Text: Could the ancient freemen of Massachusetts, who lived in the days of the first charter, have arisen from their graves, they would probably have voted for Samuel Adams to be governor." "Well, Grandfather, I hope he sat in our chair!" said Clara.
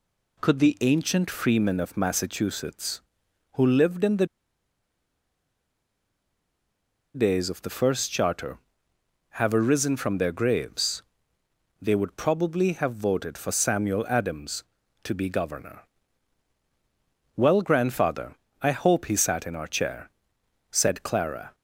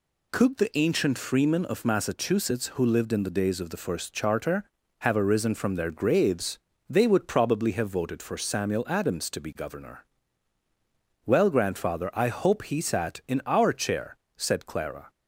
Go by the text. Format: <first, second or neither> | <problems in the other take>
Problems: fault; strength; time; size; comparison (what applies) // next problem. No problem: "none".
second | pauses between "the" and "days"; strong; at 4.2 s; 2.8 s long